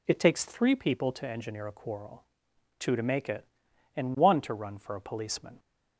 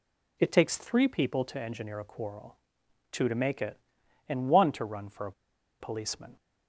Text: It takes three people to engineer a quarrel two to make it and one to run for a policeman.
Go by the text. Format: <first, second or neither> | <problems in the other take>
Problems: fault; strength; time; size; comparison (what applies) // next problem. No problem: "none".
first | pauses between "quarrel" and "two"; noticeable; at 2.5 s; 0.52 s long; noticeable in the first // pauses between "a" and "policeman"; noticeable; at 5.3 s; 0.48 s long